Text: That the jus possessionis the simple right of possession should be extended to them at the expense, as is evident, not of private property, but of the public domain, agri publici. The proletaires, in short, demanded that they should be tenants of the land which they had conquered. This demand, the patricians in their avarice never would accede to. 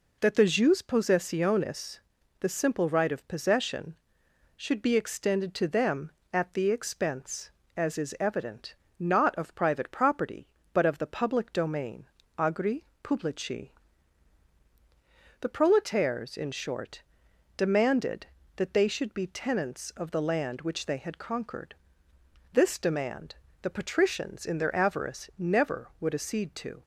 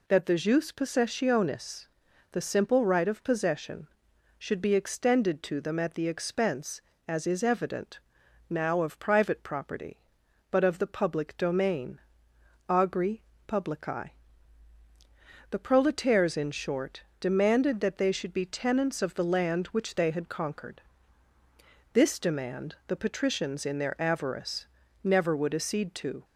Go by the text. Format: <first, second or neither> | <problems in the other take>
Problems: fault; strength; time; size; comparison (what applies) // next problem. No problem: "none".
first | pauses between "possessionis" and "the"; noticeable; at 1.8 s; 0.46 s long; also in the first // says "now" for "not"; at 8.5 s // pauses between "agri" and "publici"; slight; at 13.2 s; 0.26 s long; slight in the first // pauses between "avarice" and "never"; slight; at 24.6 s; 0.36 s long